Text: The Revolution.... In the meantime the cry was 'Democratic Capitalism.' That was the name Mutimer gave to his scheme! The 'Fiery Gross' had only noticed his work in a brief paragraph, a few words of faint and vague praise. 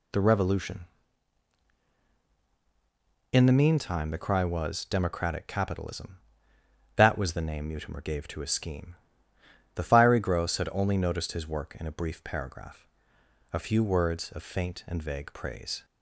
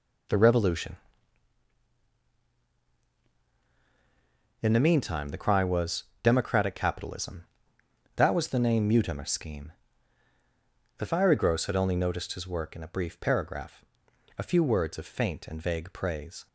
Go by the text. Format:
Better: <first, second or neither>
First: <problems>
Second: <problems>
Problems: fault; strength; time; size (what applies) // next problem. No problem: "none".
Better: first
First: none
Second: pauses between "was" and "Democratic"; slight; at 6.0 s; 0.20 s long // skips "gave to his"; at 9.2 s